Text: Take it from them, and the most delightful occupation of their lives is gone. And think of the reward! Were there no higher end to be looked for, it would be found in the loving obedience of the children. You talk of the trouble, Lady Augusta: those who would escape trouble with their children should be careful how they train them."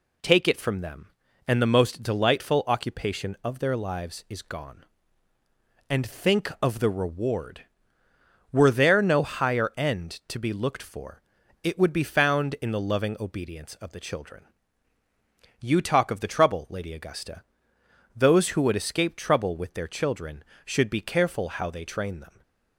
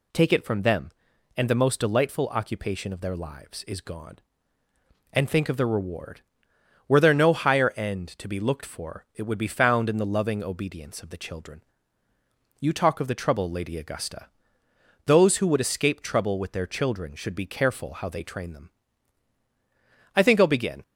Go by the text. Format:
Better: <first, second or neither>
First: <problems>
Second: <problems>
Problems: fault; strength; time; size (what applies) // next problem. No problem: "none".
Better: first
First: none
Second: goes on to say "I think I'll begin"; noticeable; from 20.1 s on; 0.66 s long